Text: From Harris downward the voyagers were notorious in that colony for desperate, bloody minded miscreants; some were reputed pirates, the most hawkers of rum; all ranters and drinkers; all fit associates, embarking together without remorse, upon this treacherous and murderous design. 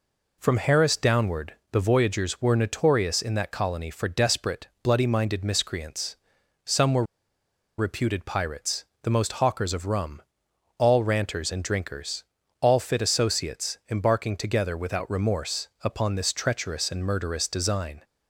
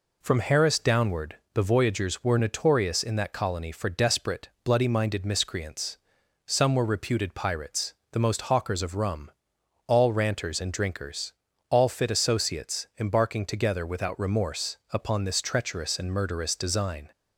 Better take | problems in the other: second | pauses between "downward" and "the"; slight; at 1.5 s; 0.18 s long; slight in the second // pauses between "were" and "reputed"; noticeable; at 7.0 s; 0.74 s long

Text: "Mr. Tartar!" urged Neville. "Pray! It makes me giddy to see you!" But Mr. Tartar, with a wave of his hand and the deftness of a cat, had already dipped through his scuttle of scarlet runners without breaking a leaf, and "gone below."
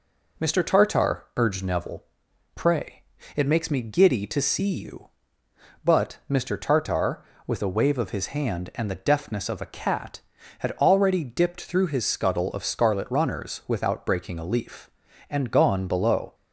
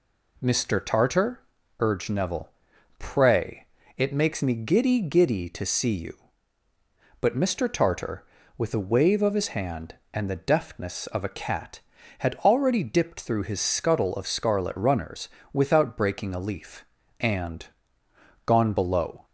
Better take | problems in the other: first | says "giddy" twice; at 5.0 s // pauses between "runners" and "without"; slight; at 15.2 s; 0.24 s long // pauses between "and" and "gone"; noticeable; at 17.6 s; 0.80 s long

